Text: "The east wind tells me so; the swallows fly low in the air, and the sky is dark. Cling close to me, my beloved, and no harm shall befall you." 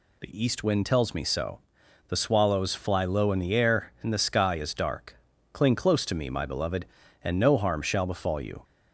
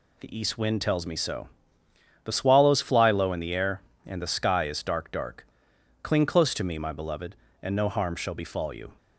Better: first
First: none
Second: says "dark" twice; at 5.1 s

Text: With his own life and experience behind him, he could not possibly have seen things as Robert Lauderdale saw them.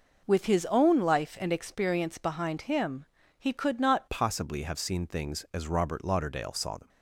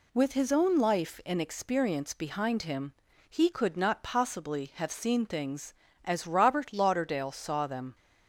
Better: second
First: changes voice at "possibly"; from 4.1 s on; 2.7 s long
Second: none

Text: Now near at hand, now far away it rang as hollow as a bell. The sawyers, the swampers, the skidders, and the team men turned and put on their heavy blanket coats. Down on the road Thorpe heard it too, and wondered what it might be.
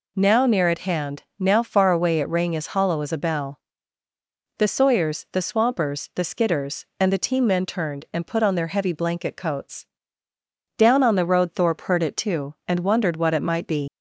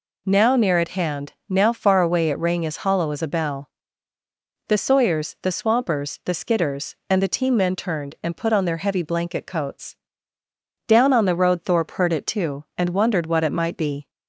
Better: second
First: leaves "be" unfinished; at 13.8 s; 120 ms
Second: none

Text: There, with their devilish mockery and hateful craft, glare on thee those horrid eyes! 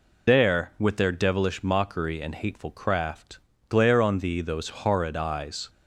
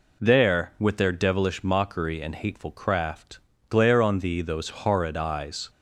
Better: second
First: loses the start of "There"; at 0.2 s; 70 ms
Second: none

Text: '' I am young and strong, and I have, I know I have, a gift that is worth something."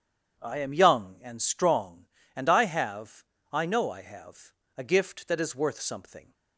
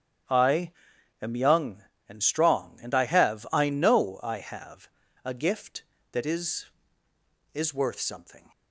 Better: first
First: starts louder than the rest; strong; until 1.4 s; 8 dB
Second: starts louder than the rest; strong; until 1.7 s; 9.5 dB // pauses between "I" and "am"; noticeable; at 0.7 s; 0.48 s long // says "is" twice; at 7.5 s

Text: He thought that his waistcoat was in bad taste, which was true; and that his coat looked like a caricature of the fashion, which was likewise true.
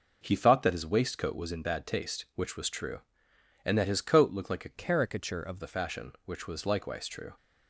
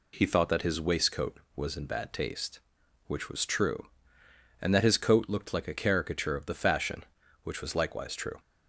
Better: second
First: changes voice from "caricature" to "of"; from 4.7 to 5.5 s; 0.8 s long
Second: none

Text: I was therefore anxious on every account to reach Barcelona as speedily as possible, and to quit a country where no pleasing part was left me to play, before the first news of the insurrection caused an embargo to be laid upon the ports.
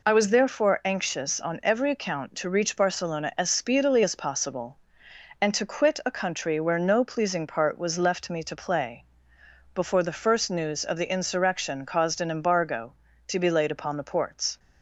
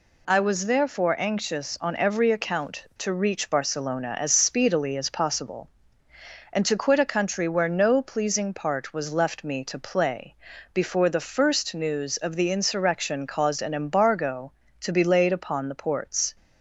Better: neither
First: none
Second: none

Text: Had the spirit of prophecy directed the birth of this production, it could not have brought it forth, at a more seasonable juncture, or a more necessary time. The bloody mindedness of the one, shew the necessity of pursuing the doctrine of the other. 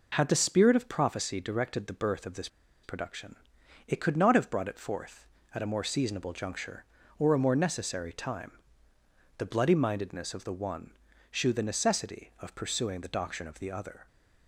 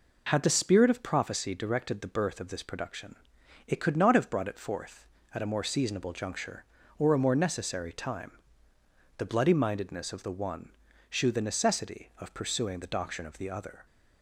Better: second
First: pauses between "this" and "production"; at 2.4 s; 0.36 s long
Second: none

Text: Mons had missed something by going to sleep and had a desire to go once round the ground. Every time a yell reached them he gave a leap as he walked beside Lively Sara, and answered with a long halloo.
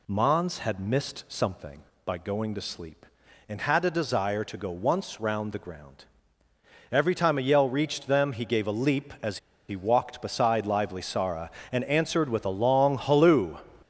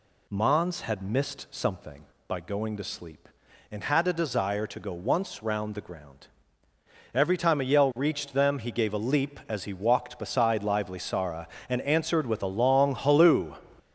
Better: second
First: pauses between "as" and "he"; slight; at 9.3 s; 0.29 s long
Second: none

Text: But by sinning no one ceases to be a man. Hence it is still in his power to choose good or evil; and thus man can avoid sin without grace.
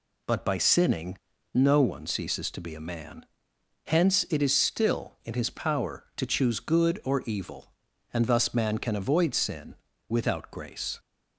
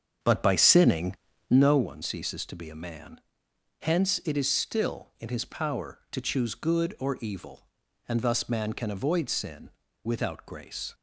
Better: first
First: pauses between "sinning" and "no"; slight; at 1.1 s; 0.35 s long // pauses between "sin" and "without"; slight; at 9.7 s; 0.34 s long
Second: starts louder than the rest; strong; until 1.8 s; 7.5 dB // pauses between "sinning" and "no"; slight; at 1.1 s; 0.34 s long // pauses between "sin" and "without"; slight; at 9.7 s; 0.34 s long

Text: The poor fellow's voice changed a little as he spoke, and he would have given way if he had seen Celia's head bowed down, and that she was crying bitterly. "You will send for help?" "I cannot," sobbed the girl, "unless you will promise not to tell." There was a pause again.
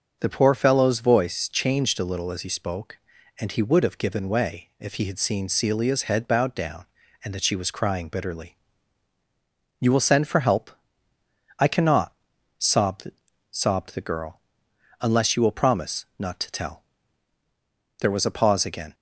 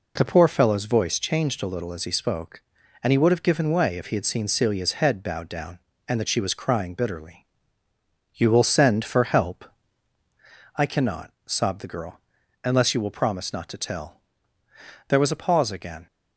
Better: second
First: starts louder than the rest; until 1.2 s; 6.5 dB // says "sobbed" twice; at 13.5 s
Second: none

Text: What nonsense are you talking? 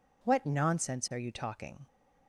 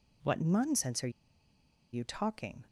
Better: first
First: none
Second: pauses between "are" and "you"; noticeable; at 1.1 s; 0.81 s long

